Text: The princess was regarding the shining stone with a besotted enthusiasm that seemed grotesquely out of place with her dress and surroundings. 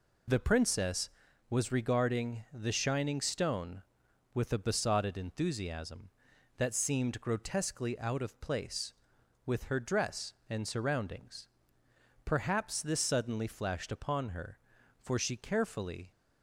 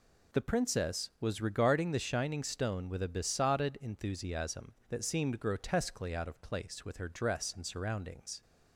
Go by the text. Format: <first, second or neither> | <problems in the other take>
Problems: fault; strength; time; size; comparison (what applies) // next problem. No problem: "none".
second | goes on to say "Perhaps this suddenly flashed upon her for she carefully"; strong; from 12.2 s on; 3.8 s long